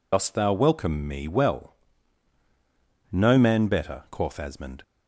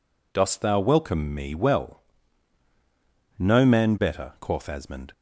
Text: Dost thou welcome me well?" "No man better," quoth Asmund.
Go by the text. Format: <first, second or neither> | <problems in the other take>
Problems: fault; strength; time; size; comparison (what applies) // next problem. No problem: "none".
second | loses the start of "Dost"; at 0.1 s; 70 ms